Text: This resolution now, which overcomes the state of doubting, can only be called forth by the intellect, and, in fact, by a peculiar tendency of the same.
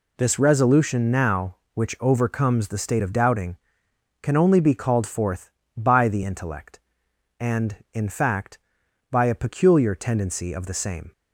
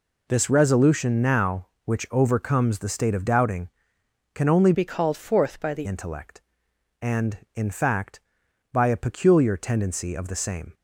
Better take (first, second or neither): first